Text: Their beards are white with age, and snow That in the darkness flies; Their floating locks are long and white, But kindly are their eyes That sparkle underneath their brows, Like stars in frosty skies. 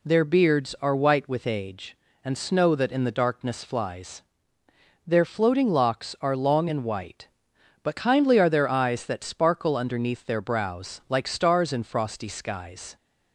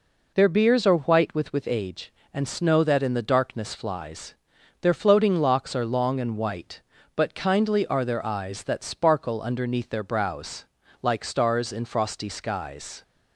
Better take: first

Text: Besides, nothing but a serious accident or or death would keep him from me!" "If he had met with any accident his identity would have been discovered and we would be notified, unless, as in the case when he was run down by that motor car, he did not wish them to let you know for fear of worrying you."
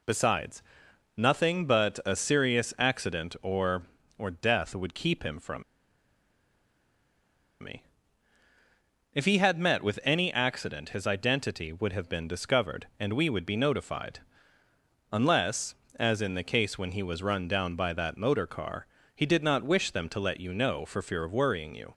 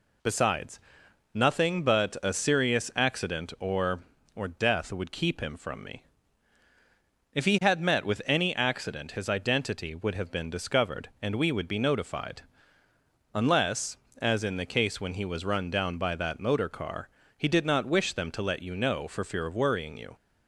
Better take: second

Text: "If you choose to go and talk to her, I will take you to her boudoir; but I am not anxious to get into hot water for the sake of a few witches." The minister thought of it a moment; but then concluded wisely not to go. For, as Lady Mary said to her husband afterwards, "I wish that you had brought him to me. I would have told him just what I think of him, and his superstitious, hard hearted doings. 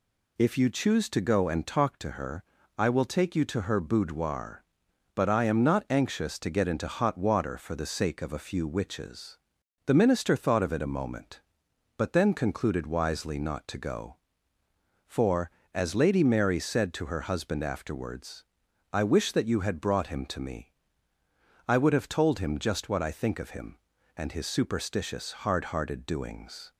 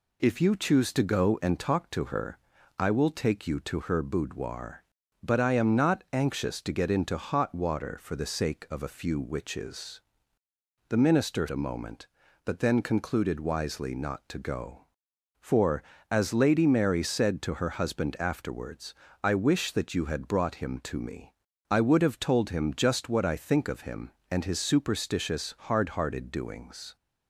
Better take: first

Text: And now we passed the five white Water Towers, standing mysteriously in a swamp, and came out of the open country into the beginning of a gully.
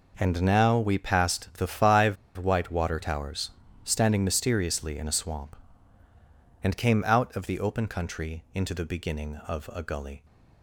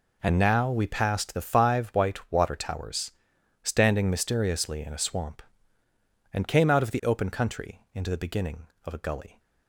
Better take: second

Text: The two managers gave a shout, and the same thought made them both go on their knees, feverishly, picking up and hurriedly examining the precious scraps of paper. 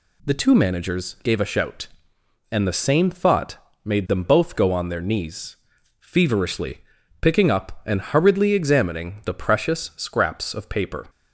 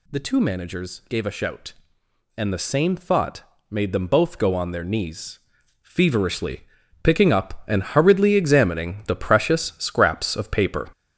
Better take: first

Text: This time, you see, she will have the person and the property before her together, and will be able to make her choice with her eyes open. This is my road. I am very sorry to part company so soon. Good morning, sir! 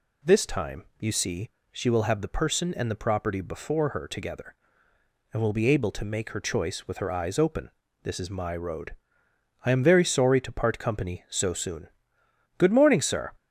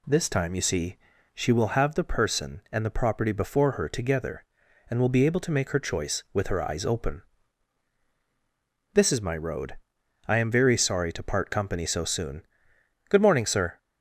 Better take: neither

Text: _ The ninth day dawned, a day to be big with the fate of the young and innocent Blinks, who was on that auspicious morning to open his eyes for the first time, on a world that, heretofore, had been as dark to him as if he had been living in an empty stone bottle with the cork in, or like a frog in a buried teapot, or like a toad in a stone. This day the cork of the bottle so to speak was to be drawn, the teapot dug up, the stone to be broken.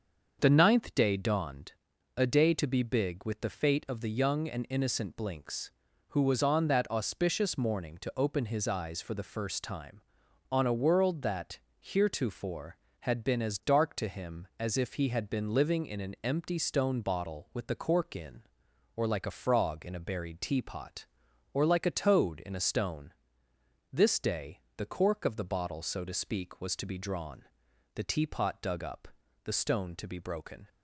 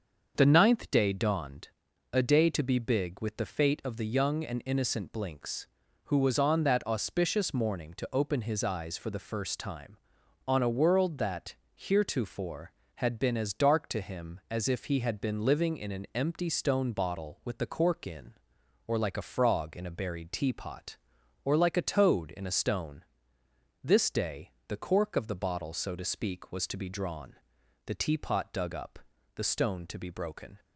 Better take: neither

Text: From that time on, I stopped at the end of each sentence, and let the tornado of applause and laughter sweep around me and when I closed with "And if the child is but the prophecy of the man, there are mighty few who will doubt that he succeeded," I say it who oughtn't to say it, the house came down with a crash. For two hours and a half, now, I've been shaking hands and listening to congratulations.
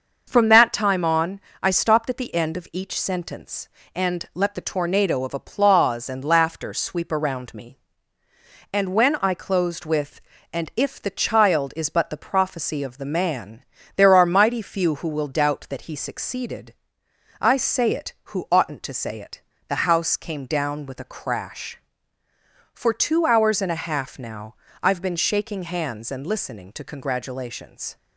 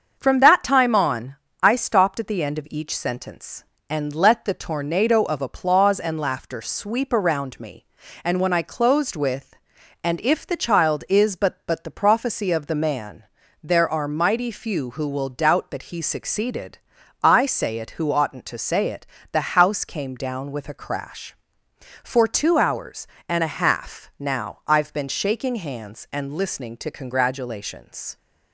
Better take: first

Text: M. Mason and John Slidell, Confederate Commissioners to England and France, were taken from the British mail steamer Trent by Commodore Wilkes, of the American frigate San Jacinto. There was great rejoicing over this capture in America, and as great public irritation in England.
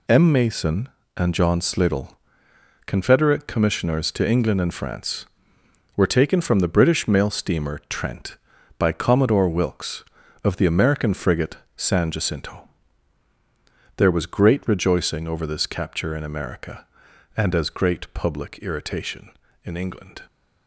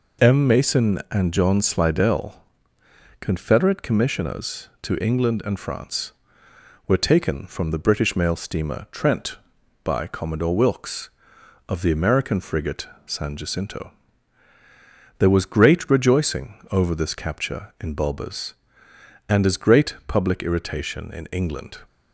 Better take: first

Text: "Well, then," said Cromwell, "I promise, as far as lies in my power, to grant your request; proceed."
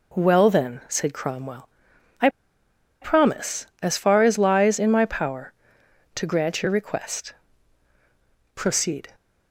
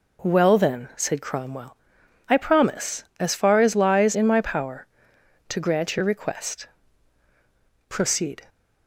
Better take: second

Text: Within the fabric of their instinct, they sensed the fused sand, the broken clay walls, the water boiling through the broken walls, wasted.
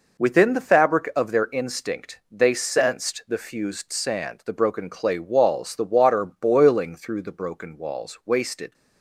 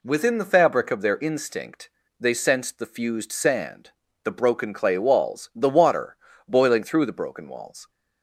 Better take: first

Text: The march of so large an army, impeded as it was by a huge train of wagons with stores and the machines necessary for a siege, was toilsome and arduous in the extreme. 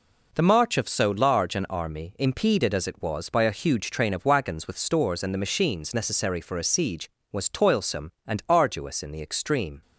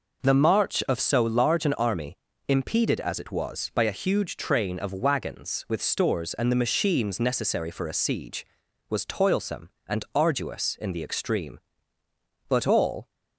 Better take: first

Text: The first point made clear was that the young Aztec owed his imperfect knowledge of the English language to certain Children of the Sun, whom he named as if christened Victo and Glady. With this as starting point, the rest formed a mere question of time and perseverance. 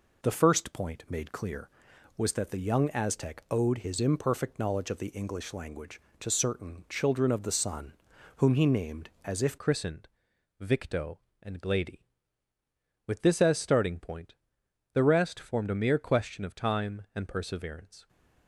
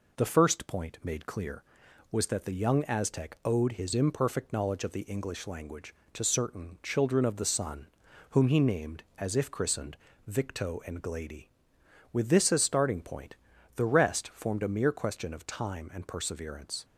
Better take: second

